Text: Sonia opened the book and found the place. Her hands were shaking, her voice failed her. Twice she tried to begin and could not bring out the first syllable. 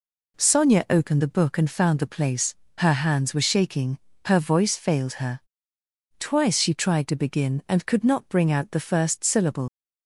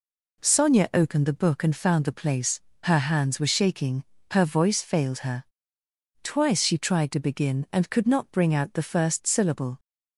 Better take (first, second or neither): second